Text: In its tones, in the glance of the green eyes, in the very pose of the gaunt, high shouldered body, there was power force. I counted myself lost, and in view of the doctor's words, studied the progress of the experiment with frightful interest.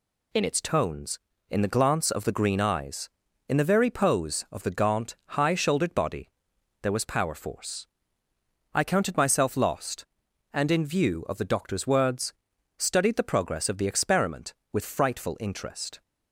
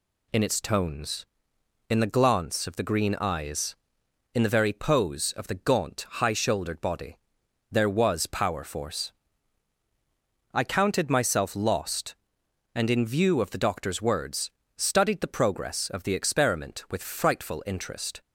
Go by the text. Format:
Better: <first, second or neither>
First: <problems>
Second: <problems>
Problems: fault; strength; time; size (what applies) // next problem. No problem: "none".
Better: neither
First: none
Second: none